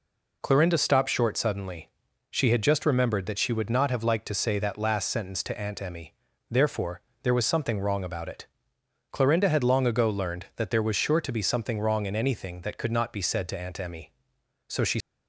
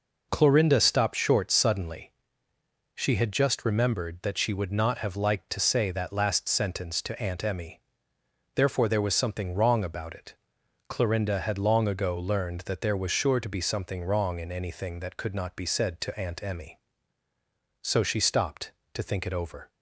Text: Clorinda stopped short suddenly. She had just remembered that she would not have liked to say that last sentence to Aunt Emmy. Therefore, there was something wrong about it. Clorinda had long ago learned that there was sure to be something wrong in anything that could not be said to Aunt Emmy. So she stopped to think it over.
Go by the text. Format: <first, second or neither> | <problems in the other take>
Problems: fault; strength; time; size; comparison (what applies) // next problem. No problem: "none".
second | stops before "stopped to think it over"; at 15.0 s